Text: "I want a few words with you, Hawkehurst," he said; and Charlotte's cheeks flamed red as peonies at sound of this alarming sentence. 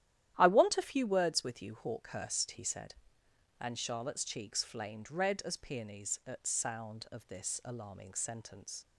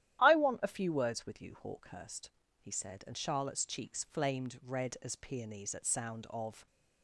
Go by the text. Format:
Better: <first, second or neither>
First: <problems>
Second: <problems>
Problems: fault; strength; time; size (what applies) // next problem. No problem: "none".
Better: first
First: starts louder than the rest; strong; until 1.3 s; 12 dB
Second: starts louder than the rest; strong; until 1.2 s; 12.5 dB // stops before "this alarming sentence"; at 6.6 s